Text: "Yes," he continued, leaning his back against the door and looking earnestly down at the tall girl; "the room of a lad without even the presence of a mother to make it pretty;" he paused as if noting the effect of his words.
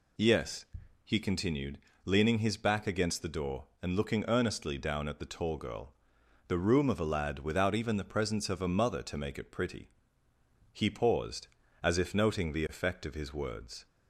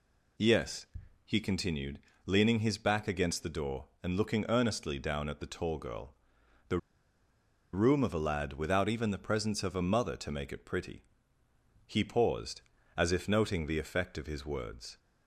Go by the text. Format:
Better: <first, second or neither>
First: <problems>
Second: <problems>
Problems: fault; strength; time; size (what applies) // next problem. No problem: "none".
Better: first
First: none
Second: pauses between "the" and "room"; noticeable; at 6.7 s; 0.96 s long